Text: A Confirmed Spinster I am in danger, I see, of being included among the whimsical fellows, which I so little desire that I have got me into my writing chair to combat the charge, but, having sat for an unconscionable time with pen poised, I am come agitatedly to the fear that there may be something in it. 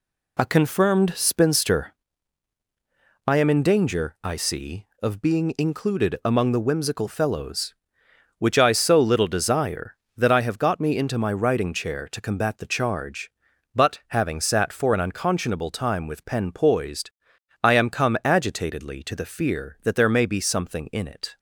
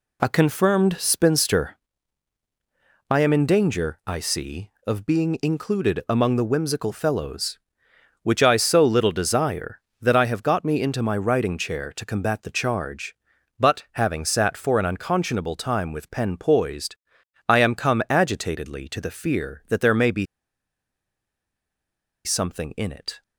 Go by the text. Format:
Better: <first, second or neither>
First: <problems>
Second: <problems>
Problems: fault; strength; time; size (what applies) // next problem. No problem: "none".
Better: first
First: pauses between "Spinster" and "I"; strong; at 1.9 s; 1.3 s long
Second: pauses between "Spinster" and "I"; strong; at 1.7 s; 1.3 s long // pauses between "be" and "something"; strong; at 20.2 s; 2.0 s long